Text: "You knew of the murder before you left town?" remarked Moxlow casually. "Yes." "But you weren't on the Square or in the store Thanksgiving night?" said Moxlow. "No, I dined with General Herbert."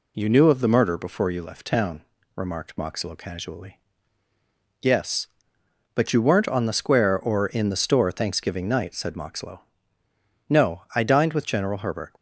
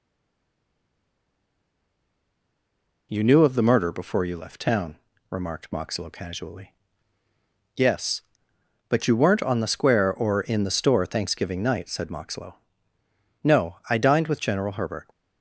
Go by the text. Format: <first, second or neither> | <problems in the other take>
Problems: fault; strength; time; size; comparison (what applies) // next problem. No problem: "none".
first | stays silent before the first word; strong; until 3.0 s; 3.0 s long